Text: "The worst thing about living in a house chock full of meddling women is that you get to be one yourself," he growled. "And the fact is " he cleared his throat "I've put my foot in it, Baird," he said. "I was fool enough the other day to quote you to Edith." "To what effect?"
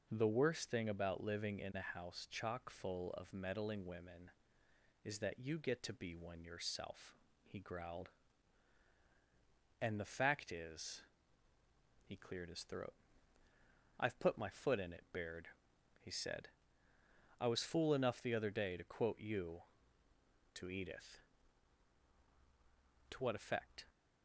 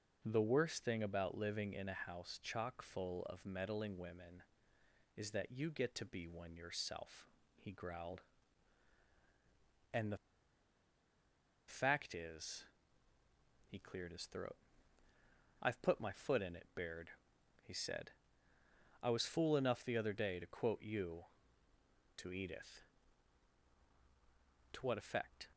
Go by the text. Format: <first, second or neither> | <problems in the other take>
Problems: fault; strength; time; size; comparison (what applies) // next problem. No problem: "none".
first | pauses between "the" and "fact"; strong; at 10.1 s; 1.5 s long // pauses between "throat" and "I've"; at 14.5 s; 1.0 s long; also in the first